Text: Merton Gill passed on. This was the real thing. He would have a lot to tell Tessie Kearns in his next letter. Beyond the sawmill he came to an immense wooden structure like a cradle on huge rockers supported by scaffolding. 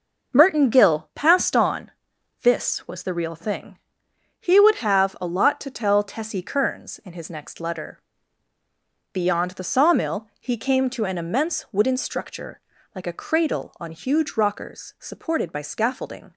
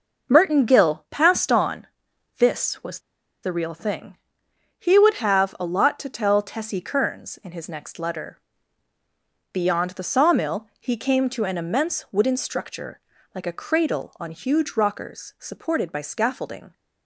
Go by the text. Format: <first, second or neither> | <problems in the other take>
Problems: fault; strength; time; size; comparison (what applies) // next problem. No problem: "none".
first | pauses between "was" and "the"; at 2.9 s; 0.43 s long // pauses between "structure" and "like"; slight; at 12.9 s; 0.34 s long; slight in the first